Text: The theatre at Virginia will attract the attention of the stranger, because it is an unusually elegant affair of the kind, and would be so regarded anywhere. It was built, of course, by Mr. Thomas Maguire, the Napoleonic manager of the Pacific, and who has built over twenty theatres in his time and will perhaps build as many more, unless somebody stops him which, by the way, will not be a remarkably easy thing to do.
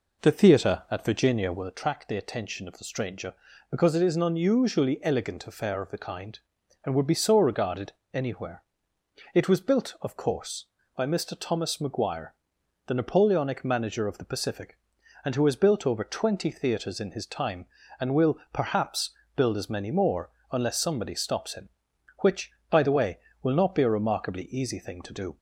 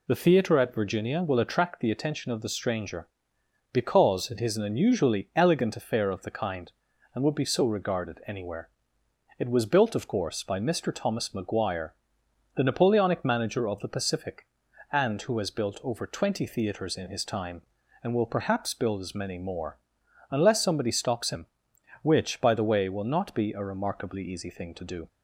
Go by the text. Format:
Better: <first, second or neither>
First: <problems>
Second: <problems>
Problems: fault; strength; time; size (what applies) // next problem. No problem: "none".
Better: second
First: starts louder than the rest; noticeable; until 1.7 s; 4.5 dB // pauses between "regarded" and "anywhere"; slight; at 7.9 s; 0.20 s long // pauses between "perhaps" and "build"; slight; at 19.1 s; 0.24 s long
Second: none